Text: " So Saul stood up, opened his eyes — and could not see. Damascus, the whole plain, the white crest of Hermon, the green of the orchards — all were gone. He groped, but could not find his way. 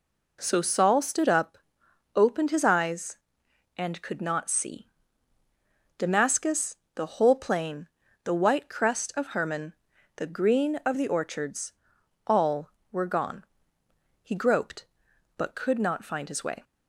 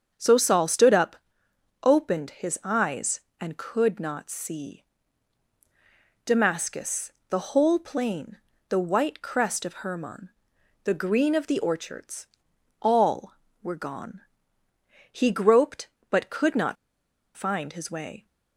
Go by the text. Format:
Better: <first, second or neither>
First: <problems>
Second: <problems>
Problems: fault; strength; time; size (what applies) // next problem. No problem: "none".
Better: first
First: none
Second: starts louder than the rest; until 1.1 s; 7 dB // pauses between "not" and "find"; noticeable; at 16.7 s; 0.59 s long